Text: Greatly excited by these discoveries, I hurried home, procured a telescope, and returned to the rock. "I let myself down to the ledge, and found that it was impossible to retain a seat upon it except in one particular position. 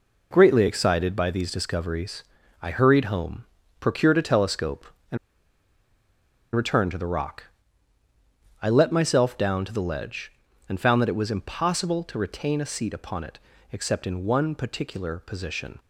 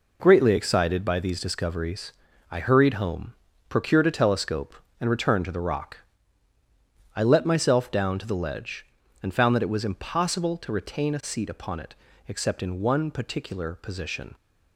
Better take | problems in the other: second | pauses between "and" and "returned"; strong; at 5.1 s; 1.3 s long // pauses between "it" and "except"; slight; at 13.3 s; 0.36 s long; slight in the second

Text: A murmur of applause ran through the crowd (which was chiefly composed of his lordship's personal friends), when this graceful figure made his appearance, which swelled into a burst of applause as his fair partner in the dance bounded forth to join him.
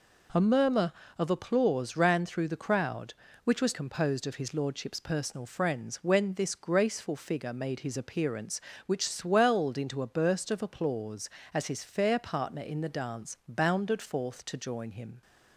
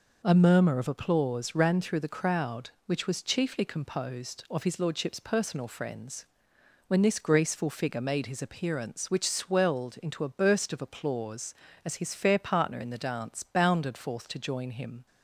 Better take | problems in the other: second | skips "chiefly"; at 3.7 s

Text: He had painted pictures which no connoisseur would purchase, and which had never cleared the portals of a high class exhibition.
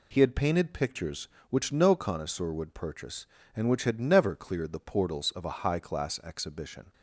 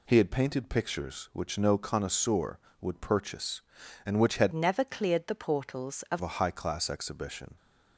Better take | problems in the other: first | changes voice from "never" to "of"; from 4.5 to 6.2 s; 1.7 s long

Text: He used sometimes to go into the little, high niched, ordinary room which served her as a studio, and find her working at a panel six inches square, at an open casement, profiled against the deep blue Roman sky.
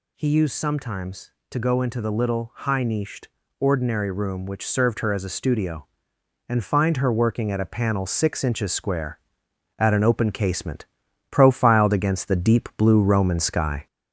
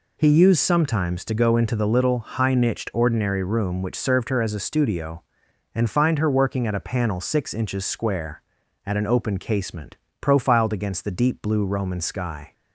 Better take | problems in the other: second | gets louder; throughout; 3.5 dB

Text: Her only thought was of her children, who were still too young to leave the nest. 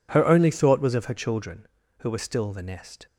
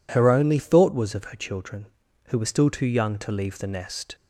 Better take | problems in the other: second | skips "too young to leave"; at 2.5 s

